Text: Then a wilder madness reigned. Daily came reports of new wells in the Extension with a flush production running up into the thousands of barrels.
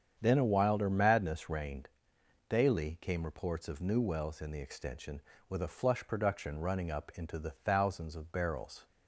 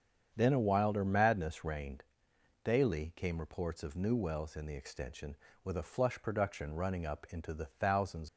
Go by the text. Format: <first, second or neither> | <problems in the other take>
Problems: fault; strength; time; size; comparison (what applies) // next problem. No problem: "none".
first | starts louder than the rest; strong; until 1.3 s; 7.5 dB; strong in the first // stops before "of barrels"; at 8.2 s